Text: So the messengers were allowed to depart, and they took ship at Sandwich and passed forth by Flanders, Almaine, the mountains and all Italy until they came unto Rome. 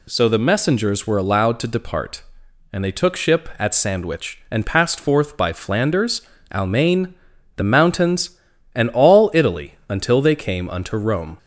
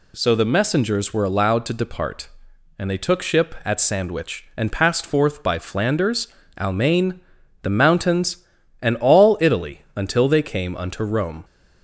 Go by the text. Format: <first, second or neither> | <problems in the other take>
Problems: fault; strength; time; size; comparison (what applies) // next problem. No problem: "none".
neither | pauses between "Italy" and "until"; slight; the same in both